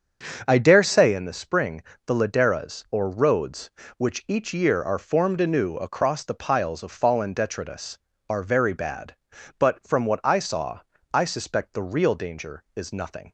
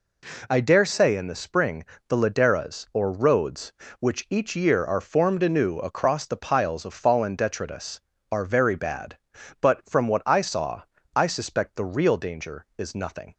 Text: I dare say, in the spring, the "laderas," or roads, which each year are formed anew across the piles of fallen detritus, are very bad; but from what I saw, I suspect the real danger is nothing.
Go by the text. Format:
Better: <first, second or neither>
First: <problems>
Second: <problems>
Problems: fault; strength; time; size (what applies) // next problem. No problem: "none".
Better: second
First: starts louder than the rest; until 1.3 s; 7 dB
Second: none